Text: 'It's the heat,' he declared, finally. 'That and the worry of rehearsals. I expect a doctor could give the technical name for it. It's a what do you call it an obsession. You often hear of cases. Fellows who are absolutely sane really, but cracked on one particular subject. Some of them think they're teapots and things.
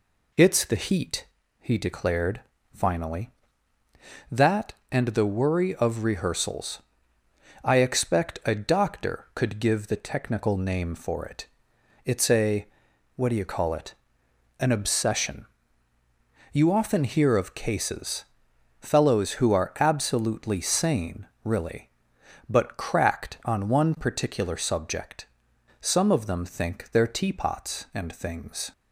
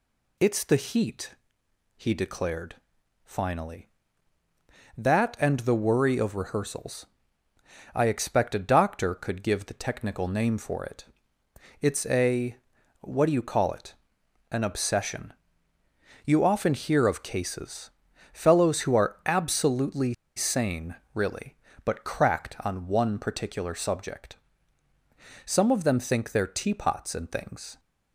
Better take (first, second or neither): first